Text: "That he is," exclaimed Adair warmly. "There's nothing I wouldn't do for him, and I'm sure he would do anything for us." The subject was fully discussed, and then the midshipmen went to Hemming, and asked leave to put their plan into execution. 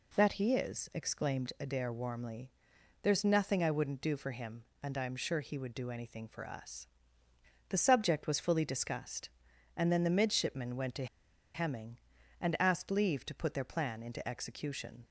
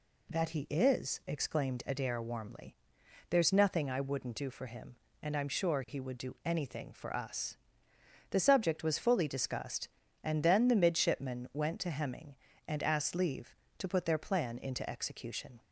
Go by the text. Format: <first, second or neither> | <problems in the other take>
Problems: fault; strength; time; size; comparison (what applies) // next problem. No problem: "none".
second | pauses between "to" and "Hemming"; noticeable; at 11.0 s; 0.48 s long